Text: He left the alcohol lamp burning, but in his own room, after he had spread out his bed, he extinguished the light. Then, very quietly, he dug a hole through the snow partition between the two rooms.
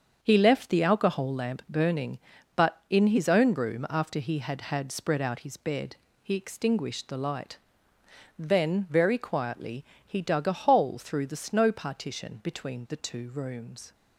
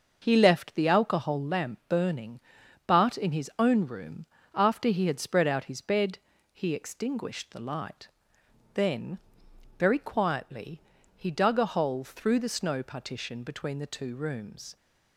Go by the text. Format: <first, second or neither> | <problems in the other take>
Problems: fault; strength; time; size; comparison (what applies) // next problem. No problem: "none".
second | starts louder than the rest; strong; until 1.2 s; 7 dB; also in the second // says "had" twice; at 4.6 s